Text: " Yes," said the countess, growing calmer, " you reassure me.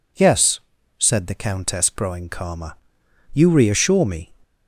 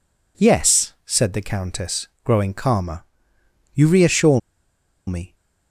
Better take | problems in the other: first | pauses between "reassure" and "me"; noticeable; at 4.3 s; 0.68 s long

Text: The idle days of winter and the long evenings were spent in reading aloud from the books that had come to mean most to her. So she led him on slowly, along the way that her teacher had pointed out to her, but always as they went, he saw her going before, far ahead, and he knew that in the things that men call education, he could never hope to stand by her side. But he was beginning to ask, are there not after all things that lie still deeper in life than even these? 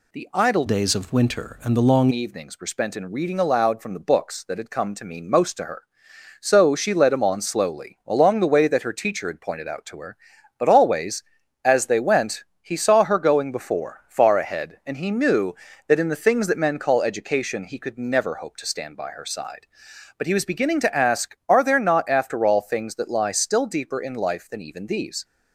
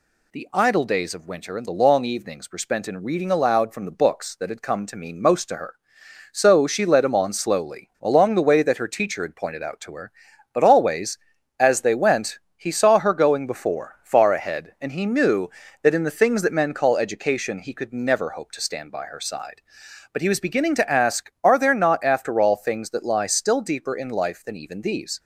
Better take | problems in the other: second | changes voice from "days" to "long"; from 0.6 to 2.0 s; 1.4 s long

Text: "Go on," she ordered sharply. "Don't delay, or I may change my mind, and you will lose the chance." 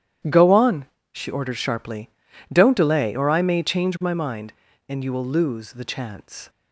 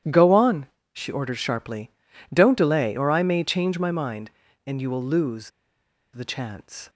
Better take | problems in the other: first | starts louder than the rest; strong; until 1.3 s; 11 dB; strong in the first // pauses between "lose" and "the"; noticeable; at 5.5 s; 0.63 s long

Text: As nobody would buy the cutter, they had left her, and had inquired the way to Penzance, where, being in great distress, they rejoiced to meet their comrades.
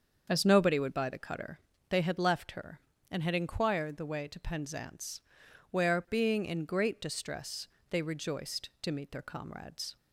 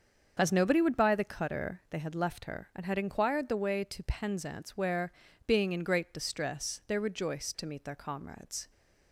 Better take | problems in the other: neither | starts louder than the rest; the same in both

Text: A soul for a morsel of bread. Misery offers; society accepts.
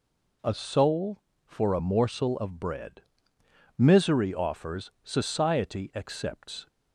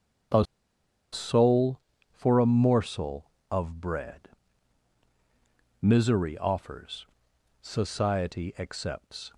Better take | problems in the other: first | starts louder than the rest; until 2.3 s; 7 dB // pauses between "A" and "soul"; noticeable; at 0.4 s; 0.67 s long

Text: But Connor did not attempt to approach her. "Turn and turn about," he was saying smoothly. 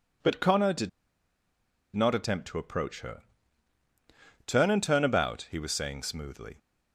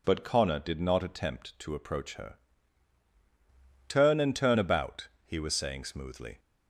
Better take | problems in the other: second | pauses between "did" and "not"; at 0.8 s; 1.0 s long

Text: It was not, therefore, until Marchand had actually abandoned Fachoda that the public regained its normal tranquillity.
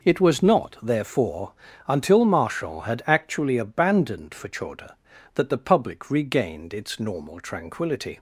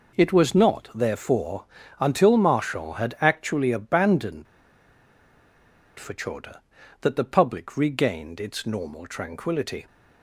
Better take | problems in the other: first | pauses between "abandoned" and "Fachoda"; strong; at 4.4 s; 1.5 s long

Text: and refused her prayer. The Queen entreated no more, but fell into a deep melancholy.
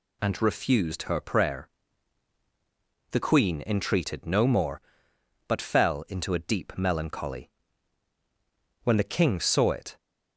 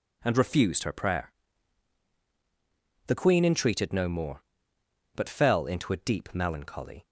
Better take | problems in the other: second | goes on to say "When the King saw it"; noticeable; from 8.8 s on; 1.1 s long

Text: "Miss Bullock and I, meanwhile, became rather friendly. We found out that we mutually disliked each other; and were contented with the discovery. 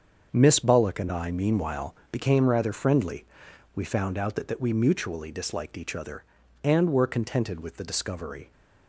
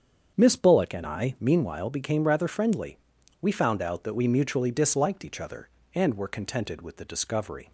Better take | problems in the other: second | starts louder than the rest; until 1.3 s; 7 dB; strong in the second // says "that" twice; at 4.4 s

